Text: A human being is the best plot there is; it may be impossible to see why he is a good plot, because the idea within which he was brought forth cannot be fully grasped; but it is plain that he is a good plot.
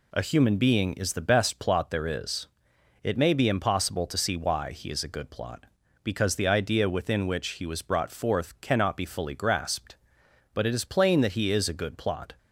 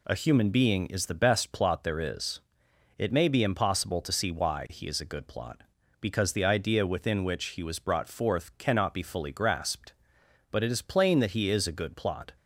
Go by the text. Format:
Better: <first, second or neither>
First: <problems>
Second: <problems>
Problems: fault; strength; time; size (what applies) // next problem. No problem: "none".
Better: neither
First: none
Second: none